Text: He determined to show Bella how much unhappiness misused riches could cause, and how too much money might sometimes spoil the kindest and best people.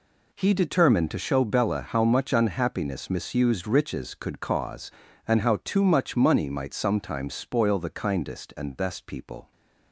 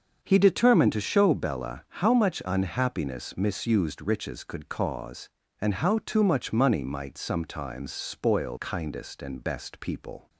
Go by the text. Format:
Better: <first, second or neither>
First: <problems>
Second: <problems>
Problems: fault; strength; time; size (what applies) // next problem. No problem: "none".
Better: first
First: none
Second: starts louder than the rest; until 1.2 s; 6.5 dB // skips "the"; at 8.5 s